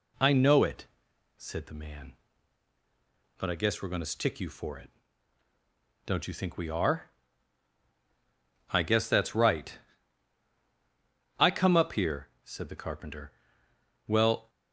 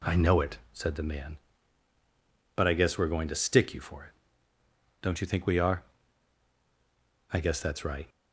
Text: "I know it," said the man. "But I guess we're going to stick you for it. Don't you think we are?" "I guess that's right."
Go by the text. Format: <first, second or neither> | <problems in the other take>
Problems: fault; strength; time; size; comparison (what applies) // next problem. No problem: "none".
second | goes on to say "I come up here said the carpenter well"; strong; from 11.3 s on; 3.1 s long